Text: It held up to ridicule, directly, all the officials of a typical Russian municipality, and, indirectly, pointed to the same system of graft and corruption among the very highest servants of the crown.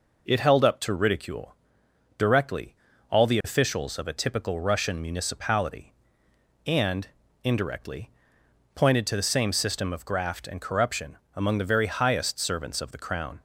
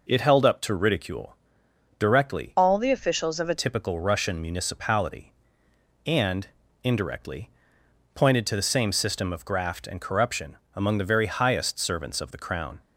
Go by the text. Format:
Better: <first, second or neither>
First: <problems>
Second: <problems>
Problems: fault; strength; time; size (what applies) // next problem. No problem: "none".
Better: first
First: pauses between "corruption" and "among"; slight; at 11.1 s; 0.18 s long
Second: changes voice from "all" to "a"; from 2.5 to 3.5 s; 1.0 s long // pauses between "corruption" and "among"; slight; at 10.5 s; 0.18 s long